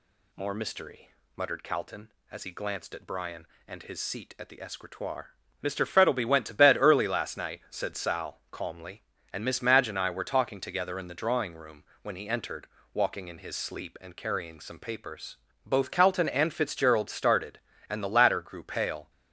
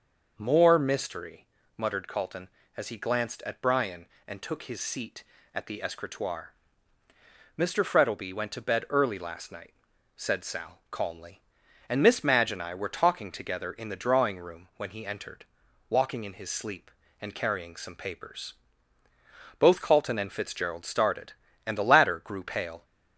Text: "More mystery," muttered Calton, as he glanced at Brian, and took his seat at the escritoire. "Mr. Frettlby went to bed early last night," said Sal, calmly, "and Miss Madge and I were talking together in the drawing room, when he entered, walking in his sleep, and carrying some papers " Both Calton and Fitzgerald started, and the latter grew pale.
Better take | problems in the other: second | skips "took"; at 3.8 s

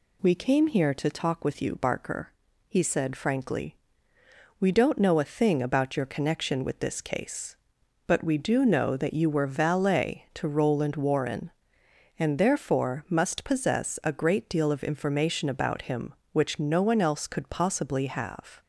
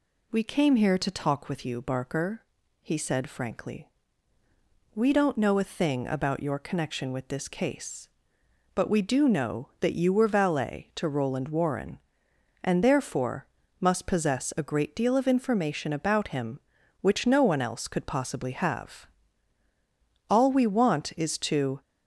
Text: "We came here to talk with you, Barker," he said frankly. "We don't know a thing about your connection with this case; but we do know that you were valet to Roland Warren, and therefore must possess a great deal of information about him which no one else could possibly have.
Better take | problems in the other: first | pauses between "therefore" and "must"; slight; at 13.4 s; 0.34 s long // goes on to say "All we want is to"; from 20.2 s on; 1.5 s long

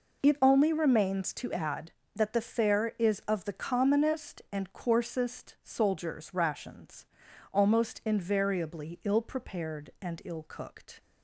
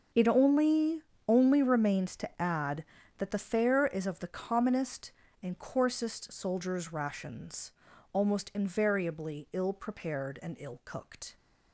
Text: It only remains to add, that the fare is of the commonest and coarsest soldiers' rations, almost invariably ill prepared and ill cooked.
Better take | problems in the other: first | starts louder than the rest; noticeable; until 1.4 s; 6 dB // says "only" twice; at 1.2 s

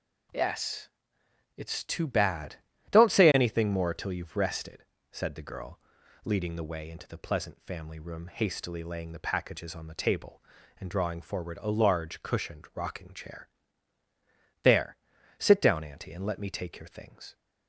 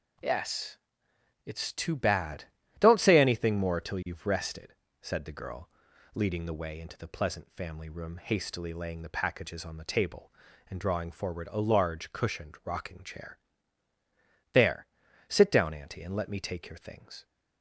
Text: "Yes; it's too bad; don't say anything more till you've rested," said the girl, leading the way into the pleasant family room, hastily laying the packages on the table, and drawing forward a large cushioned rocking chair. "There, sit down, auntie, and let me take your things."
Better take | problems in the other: neither | none

